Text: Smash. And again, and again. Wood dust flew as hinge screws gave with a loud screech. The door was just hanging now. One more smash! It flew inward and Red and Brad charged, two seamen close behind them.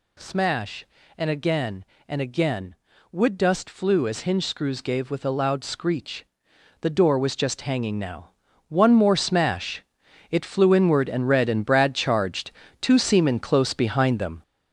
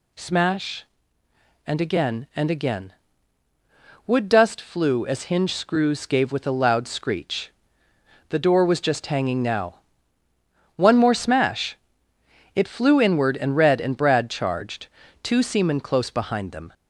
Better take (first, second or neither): second